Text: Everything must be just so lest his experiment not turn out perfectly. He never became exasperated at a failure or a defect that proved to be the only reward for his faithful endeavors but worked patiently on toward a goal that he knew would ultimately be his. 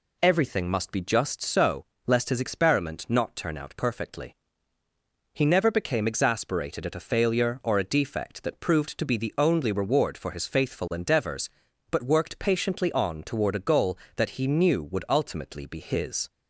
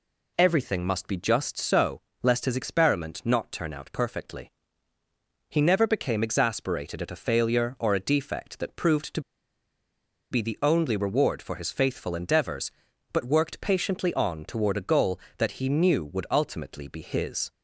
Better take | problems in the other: first | pauses between "so" and "lest"; slight; at 2.0 s; 0.22 s long; slight in the first // pauses between "to" and "be"; at 9.2 s; 1.1 s long

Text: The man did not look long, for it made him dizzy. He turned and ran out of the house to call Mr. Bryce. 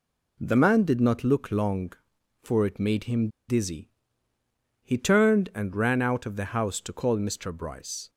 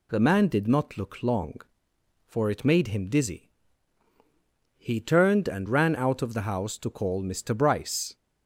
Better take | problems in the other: second | pauses between "him" and "dizzy"; slight; at 3.2 s; 0.20 s long

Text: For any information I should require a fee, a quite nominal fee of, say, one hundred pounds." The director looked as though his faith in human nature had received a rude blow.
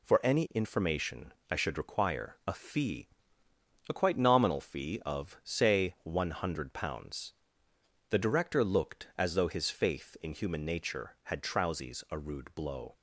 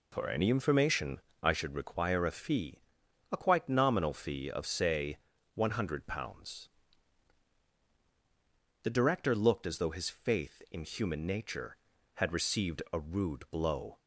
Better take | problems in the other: second | pauses between "information" and "I"; slight; at 1.3 s; 0.18 s long; slight in the second // says "trousies" for "received"; at 11.4 s

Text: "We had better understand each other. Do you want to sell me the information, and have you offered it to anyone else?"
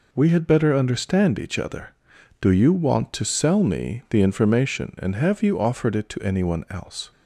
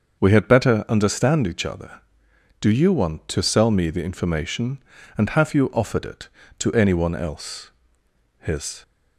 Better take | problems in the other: first | starts louder than the rest; until 1.2 s; 6.5 dB // goes on to say "His"; slight; from 8.3 s on; 0.44 s long

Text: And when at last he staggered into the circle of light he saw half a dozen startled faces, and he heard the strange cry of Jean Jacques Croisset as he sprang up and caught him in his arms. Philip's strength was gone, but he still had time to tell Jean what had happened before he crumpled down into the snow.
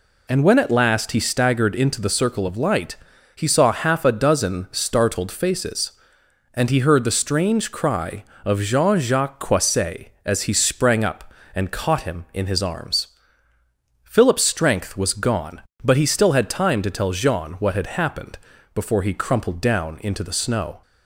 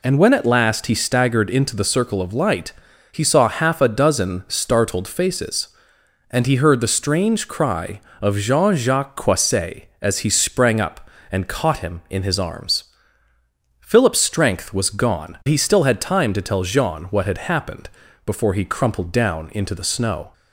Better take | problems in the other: first | pauses between "light" and "he"; at 2.7 s; 0.38 s long; also in the first // skips "but"; at 15.4 s // pauses between "happened" and "before"; slight; at 17.8 s; 0.36 s long; slight in the first

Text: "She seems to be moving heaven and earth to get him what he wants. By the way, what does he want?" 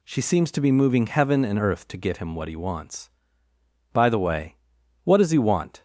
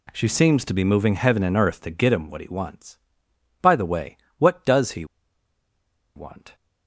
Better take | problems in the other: first | pauses between "he" and "want"; at 5.0 s; 1.1 s long

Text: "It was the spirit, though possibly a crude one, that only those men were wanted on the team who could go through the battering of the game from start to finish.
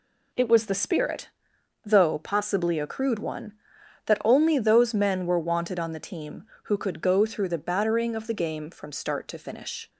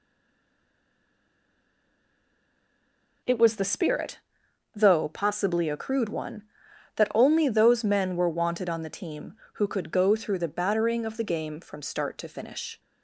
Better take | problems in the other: first | stays silent before the first word; strong; until 3.2 s; 3.2 s long

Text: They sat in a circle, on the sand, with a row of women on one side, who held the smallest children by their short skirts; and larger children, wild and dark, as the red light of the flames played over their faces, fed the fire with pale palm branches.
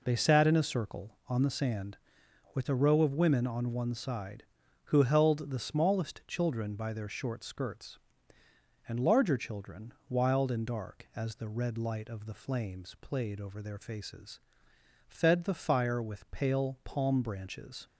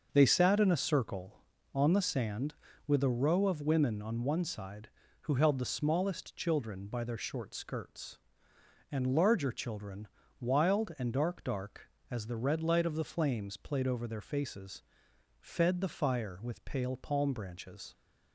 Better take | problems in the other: first | starts louder than the rest; until 1.1 s; 6.5 dB // says "dark" twice; at 11.4 s

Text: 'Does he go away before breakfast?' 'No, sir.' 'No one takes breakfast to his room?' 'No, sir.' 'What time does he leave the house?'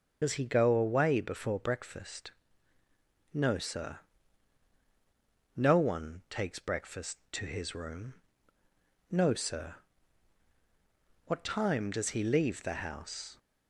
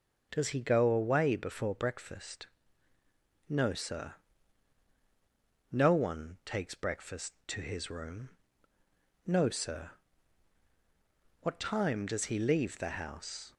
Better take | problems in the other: second | loses the start of "Does"; at 0.2 s; 60 ms // starts louder than the rest; until 1.2 s; 7 dB; also in the second

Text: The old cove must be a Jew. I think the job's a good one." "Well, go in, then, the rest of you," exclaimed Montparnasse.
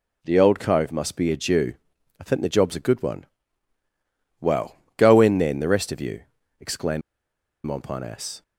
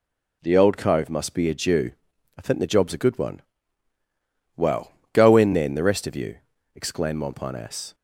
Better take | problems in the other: second | pauses between "exclaimed" and "Montparnasse"; noticeable; at 7.0 s; 0.64 s long

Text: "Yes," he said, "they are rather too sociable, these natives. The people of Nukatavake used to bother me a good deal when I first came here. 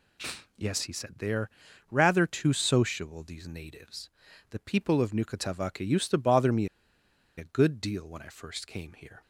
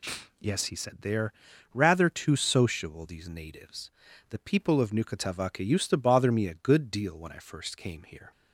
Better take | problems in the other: second | pauses between "are" and "rather"; at 1.4 s; 0.44 s long; also in the second // pauses between "me" and "a"; noticeable; at 6.6 s; 0.69 s long

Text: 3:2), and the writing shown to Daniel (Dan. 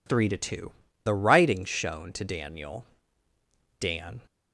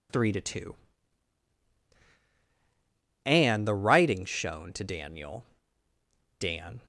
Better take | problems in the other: second | skips "and"; at 0.8 s

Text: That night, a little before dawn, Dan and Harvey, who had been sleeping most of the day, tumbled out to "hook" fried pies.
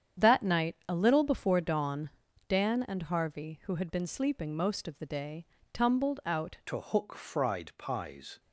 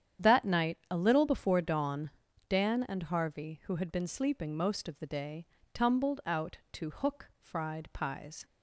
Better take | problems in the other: second | starts louder than the rest; strong; until 1.3 s; 8.5 dB; strong in the second // changes voice at "to"; from 6.6 s on; 1.7 s long

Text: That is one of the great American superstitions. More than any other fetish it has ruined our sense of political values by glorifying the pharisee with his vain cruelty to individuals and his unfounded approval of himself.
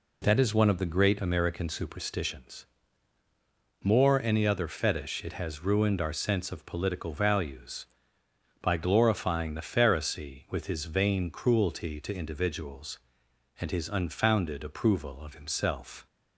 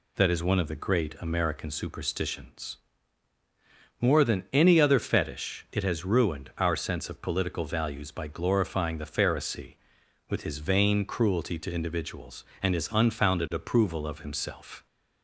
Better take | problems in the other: second | skips "than"; at 4.2 s

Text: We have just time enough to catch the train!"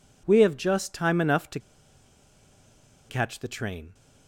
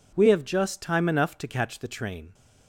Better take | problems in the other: second | pauses between "to" and "catch"; strong; at 1.5 s; 1.5 s long

